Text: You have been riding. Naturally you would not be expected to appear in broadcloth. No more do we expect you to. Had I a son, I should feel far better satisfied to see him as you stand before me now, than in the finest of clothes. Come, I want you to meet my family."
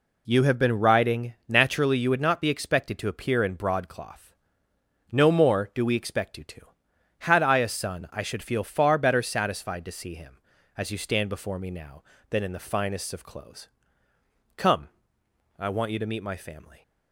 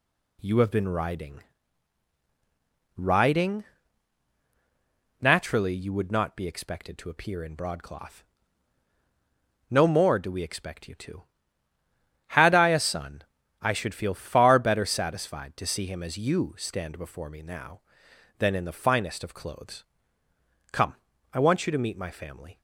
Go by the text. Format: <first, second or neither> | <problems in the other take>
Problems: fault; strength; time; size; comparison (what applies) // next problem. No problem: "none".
first | says "riding" twice; at 3.0 s